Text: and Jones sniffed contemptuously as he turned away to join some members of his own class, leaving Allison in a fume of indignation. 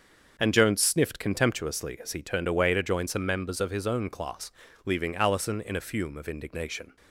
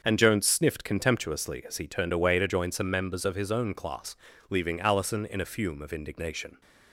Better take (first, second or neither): neither